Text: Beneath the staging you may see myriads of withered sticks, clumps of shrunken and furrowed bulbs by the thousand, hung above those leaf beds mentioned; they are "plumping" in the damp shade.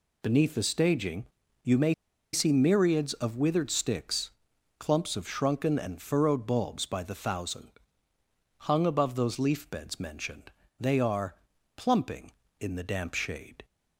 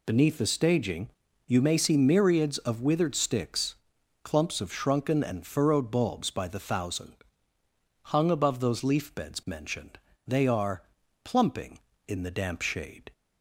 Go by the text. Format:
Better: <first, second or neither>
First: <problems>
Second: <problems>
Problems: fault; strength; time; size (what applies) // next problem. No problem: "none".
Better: second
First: pauses between "staging" and "you"; slight; at 1.2 s; 0.36 s long // pauses between "may" and "see"; at 1.9 s; 0.39 s long // pauses between "are" and "plumping"; at 11.3 s; 0.42 s long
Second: pauses between "staging" and "you"; slight; at 1.0 s; 0.36 s long // pauses between "are" and "plumping"; at 10.8 s; 0.42 s long